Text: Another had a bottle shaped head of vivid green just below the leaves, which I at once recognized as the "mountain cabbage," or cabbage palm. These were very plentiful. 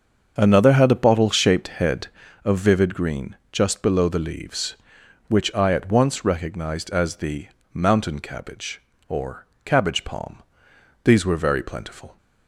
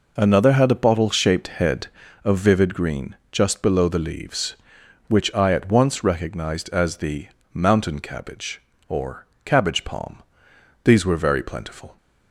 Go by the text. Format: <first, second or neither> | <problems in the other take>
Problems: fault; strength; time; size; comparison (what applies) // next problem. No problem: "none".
second | starts louder than the rest; until 1.7 s; 6.5 dB // pauses between "green" and "just"; slight; at 3.3 s; 0.16 s long; slight in the second // pauses between "the" and "mountain"; slight; at 7.4 s; 0.26 s long; slight in the second // pauses between "or" and "cabbage"; slight; at 9.4 s; 0.18 s long; slight in the second